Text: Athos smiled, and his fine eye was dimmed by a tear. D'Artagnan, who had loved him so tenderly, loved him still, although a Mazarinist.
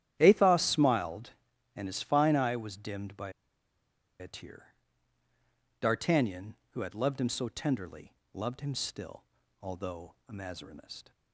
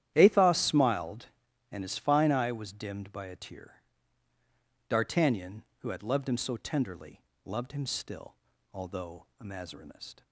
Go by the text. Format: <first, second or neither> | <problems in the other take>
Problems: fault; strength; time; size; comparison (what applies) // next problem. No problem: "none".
second | starts louder than the rest; strong; until 1.2 s; 11 dB; strong in the second // pauses between "by" and "a"; noticeable; at 3.3 s; 0.88 s long // pauses between "although" and "a"; slight; at 10.1 s; 0.16 s long; slight in the second